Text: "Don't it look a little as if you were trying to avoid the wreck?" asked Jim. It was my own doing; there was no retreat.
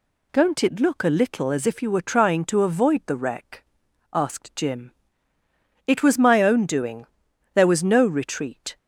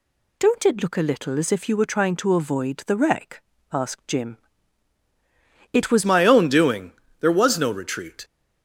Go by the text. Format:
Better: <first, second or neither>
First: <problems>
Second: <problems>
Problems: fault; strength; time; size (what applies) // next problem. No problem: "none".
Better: first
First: none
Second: changes voice at "my"; from 6.0 s on; 2.2 s long